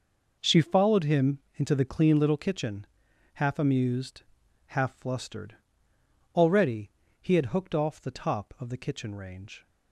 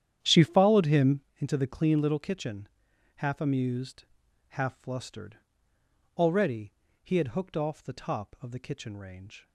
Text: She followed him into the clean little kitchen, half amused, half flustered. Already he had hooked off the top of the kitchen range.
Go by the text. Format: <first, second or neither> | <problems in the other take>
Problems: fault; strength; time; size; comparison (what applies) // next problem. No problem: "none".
first | starts louder than the rest; strong; until 1.3 s; 10 dB // pauses between "Already" and "he"; slight; at 6.7 s; 0.28 s long; slight in the first